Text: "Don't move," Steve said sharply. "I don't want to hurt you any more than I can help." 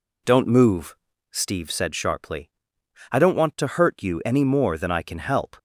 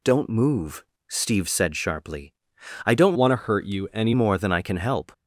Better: first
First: none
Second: changes voice from "want" to "any"; from 3.1 to 4.1 s; 1.0 s long

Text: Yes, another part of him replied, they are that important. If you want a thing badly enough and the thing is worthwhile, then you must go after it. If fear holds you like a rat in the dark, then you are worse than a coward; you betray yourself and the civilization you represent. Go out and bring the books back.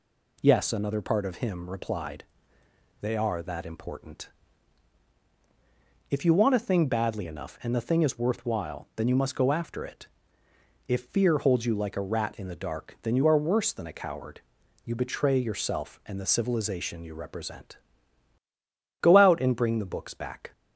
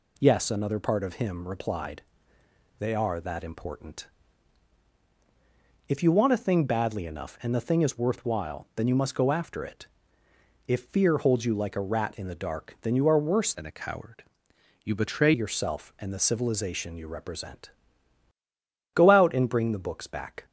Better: first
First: none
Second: changes voice from "than" to "betray"; from 13.5 to 15.3 s; 1.8 s long

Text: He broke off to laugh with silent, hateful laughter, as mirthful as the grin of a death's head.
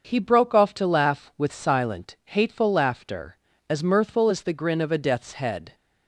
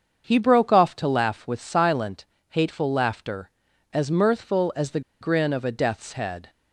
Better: first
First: starts louder than the rest; until 1.1 s; 6.5 dB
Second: starts louder than the rest; until 1.2 s; 7 dB // pauses between "the" and "grin"; slight; at 5.0 s; 0.20 s long

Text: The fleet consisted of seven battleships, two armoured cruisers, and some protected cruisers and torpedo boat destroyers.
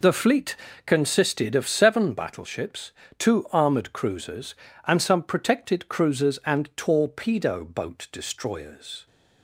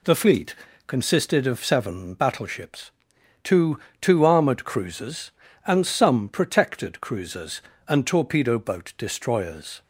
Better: first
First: pauses between "fleet" and "consisted"; slight; at 0.5 s; 0.30 s long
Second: pauses between "fleet" and "consisted"; slight; at 0.5 s; 0.30 s long // says "two" twice; at 4.0 s

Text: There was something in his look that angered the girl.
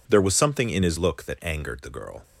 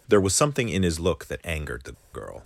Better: first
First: none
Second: pauses between "the" and "girl"; slight; at 1.9 s; 0.21 s long

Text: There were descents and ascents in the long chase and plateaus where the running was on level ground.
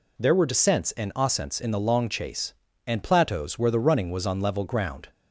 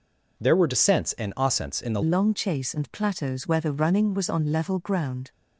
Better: first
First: none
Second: changes voice at "long"; from 2.0 s on; 3.3 s long

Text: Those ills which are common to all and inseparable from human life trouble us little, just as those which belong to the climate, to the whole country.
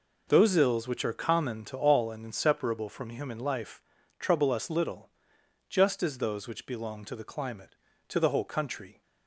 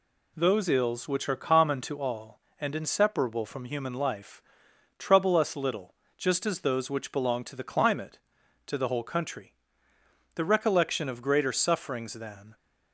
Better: first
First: pauses between "life" and "trouble"; at 3.8 s; 0.38 s long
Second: pauses between "life" and "trouble"; noticeable; at 4.4 s; 0.56 s long // goes on to say "The recollection of greater sufferings than"; strong; from 10.3 s on; 2.2 s long

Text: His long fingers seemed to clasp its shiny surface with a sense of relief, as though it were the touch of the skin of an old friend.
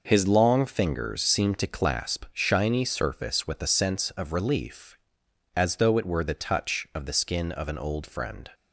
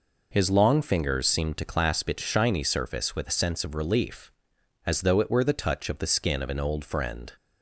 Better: second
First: skips "its"; at 2.2 s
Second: none

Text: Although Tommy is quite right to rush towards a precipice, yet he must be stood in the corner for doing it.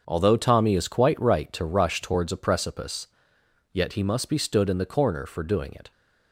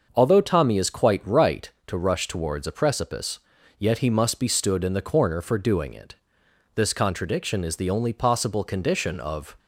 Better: first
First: starts louder than the rest; until 1.0 s; 6.5 dB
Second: starts louder than the rest; until 1.1 s; 6 dB // goes on to say "This contradiction is the only possible condition of"; strong; from 6.7 s on; 2.8 s long

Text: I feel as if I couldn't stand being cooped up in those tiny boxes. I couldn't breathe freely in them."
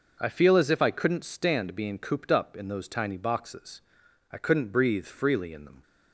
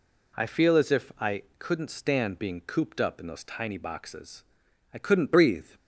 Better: first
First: none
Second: pauses between "I" and "couldn't"; slight; at 1.4 s; 0.16 s long // stops before "freely in them"; at 5.7 s

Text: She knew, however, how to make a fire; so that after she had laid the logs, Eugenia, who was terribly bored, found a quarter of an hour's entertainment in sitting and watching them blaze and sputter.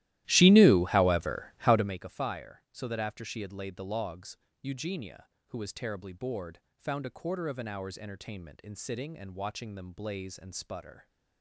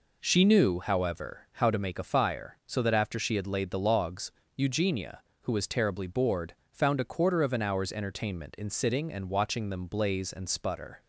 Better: second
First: starts louder than the rest; strong; until 2.1 s; 15 dB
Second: none

